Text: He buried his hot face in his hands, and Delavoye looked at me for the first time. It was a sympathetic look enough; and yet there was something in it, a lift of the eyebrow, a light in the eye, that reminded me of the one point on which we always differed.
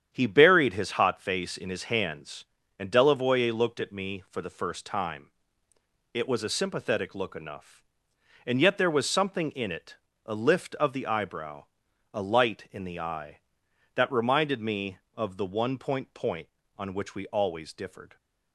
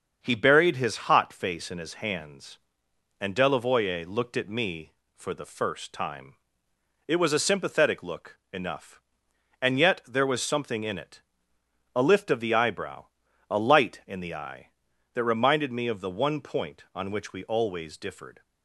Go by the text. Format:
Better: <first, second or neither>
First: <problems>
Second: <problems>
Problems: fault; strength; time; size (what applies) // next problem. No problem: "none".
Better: second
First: starts louder than the rest; strong; until 1.1 s; 9 dB // says "point" twice; at 16.1 s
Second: starts louder than the rest; until 1.2 s; 6.5 dB